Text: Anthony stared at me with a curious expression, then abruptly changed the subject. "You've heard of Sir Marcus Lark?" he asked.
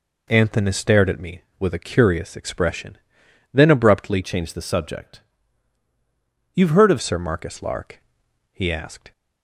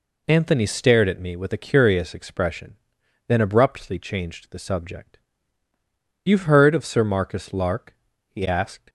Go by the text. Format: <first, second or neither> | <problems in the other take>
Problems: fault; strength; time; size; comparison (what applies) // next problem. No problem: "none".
second | changes voice from "changed" to "of"; from 4.2 to 6.9 s; 2.7 s long